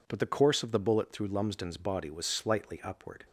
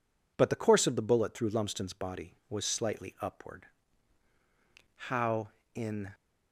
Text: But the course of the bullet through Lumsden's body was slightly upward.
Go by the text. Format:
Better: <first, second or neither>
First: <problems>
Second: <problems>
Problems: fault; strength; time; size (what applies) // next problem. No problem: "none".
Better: first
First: none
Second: goes on to say "How in"; noticeable; from 5.0 s on; 1.0 s long